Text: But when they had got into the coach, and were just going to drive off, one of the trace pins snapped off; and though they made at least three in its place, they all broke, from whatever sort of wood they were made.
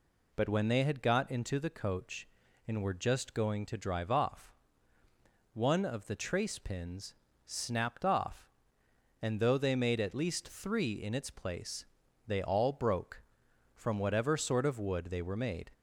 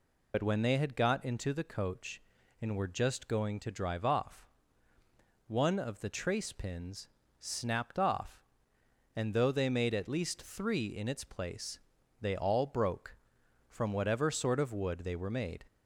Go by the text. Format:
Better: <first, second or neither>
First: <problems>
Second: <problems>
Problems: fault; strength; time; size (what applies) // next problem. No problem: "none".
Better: first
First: pauses between "pins" and "snapped"; slight; at 7.1 s; 0.32 s long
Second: loses the start of "But"; at 0.3 s; 60 ms // pauses between "pins" and "snapped"; slight; at 7.0 s; 0.32 s long